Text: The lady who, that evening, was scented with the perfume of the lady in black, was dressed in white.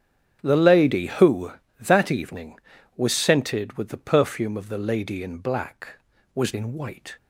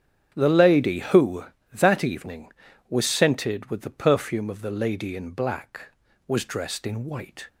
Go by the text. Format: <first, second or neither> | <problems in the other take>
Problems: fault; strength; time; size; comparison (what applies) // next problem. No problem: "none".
second | starts louder than the rest; strong; until 1.4 s; 8.5 dB; strong in the second // skips "dressed"; at 6.5 s